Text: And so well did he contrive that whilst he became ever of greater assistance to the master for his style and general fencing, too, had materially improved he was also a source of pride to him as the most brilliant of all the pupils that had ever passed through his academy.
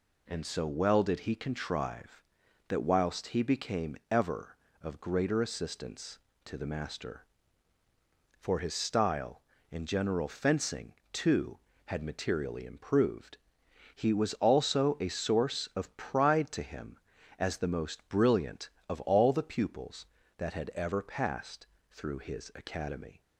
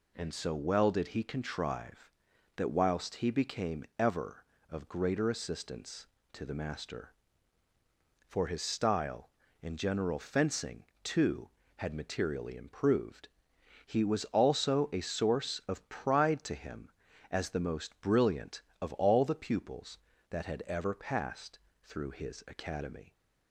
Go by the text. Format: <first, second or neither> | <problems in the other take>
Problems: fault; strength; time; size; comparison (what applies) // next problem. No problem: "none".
neither | pauses between "improved" and "he"; noticeable; the same in both // pauses between "passed" and "through"; slight; the same in both